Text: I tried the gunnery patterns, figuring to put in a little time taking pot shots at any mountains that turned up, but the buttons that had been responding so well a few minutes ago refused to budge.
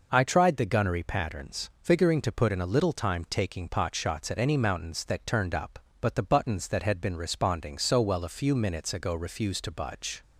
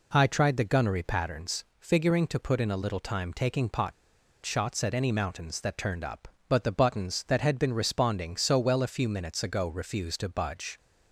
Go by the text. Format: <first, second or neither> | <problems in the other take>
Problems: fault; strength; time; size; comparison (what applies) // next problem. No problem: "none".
first | pauses between "pot" and "shots"; noticeable; at 3.9 s; 0.52 s long